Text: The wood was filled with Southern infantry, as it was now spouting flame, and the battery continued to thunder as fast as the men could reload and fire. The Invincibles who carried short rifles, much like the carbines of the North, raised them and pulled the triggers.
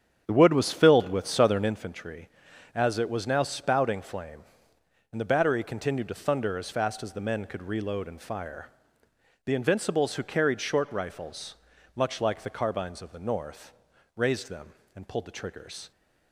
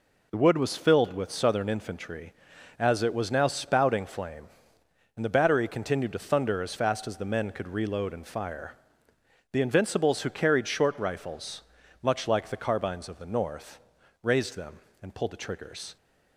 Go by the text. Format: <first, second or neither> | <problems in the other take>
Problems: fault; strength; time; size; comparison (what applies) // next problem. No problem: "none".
second | starts louder than the rest; strong; until 1.8 s; 8 dB